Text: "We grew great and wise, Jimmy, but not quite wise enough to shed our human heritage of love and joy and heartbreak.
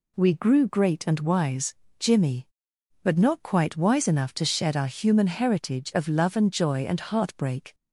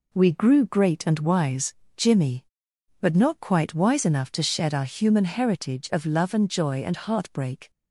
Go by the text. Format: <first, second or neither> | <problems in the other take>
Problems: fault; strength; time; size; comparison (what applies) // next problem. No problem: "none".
first | gets quieter; throughout; 6.5 dB